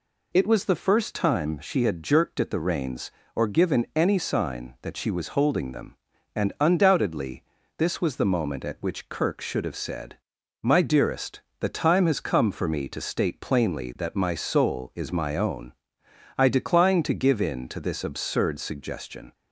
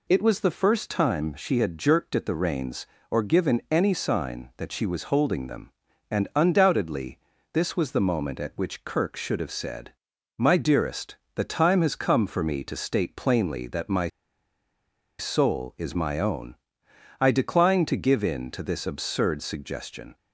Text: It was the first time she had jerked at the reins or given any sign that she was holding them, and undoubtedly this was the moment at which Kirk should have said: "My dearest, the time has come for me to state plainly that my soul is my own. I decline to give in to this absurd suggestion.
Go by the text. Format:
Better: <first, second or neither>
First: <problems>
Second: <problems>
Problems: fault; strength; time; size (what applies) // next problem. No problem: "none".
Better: first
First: pauses between "undoubtedly" and "this"; slight; at 7.4 s; 0.32 s long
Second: pauses between "undoubtedly" and "this"; slight; at 7.1 s; 0.32 s long // pauses between "my" and "soul"; at 14.0 s; 1.1 s long